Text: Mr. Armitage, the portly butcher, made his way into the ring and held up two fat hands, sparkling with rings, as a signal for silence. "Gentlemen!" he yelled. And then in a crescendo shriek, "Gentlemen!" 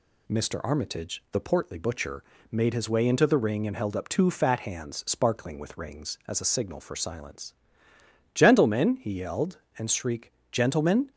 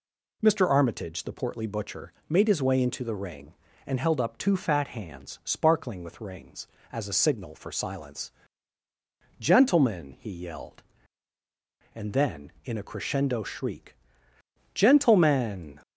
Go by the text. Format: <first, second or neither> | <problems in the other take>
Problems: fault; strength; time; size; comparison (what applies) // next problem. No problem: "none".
second | skips "then in a crescendo"; at 9.8 s